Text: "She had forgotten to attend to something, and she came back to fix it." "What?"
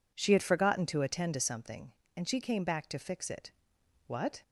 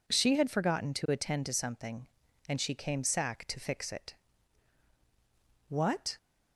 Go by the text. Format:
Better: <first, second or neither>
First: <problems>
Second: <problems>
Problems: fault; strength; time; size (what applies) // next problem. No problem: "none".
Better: first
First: none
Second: says "sack" for "back"; at 3.0 s